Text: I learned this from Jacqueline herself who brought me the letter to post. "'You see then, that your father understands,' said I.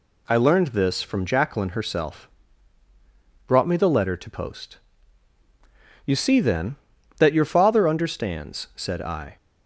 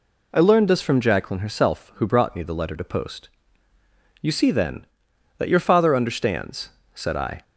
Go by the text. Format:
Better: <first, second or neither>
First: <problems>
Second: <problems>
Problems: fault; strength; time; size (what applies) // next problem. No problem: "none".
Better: second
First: skips "who"; at 2.8 s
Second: none